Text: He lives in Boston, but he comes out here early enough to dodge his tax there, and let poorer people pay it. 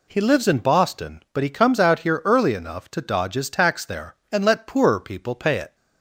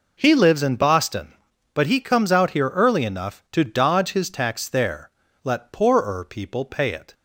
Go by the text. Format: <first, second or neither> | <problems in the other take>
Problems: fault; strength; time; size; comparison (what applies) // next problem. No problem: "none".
first | skips "and"; at 5.2 s